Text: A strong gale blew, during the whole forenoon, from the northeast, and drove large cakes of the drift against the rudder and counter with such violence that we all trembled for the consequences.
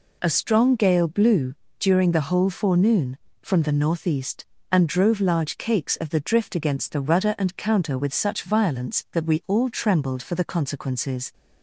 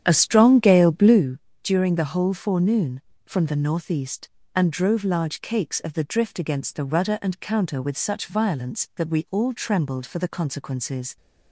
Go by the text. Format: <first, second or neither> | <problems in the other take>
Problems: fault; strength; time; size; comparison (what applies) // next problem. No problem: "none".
first | starts louder than the rest; strong; until 1.3 s; 9.5 dB